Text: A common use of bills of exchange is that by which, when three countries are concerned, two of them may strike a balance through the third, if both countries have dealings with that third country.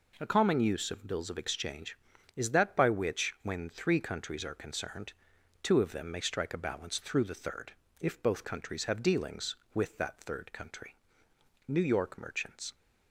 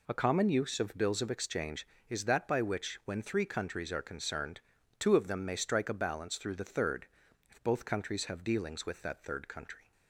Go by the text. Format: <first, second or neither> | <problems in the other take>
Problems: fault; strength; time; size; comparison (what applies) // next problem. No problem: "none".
second | goes on to say "New York merchants"; noticeable; from 11.6 s on; 1.0 s long